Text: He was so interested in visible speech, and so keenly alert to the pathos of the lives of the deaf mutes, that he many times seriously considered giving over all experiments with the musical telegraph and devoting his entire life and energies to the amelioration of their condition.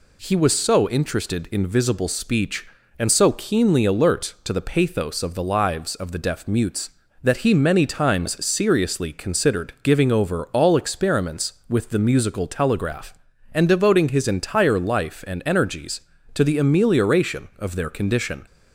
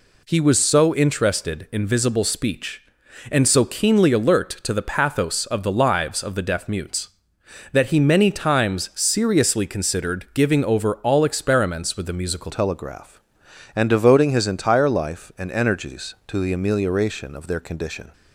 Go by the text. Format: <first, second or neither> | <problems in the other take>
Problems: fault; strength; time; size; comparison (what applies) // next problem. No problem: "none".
first | changes voice at "telegraph"; from 12.4 s on; 5.7 s long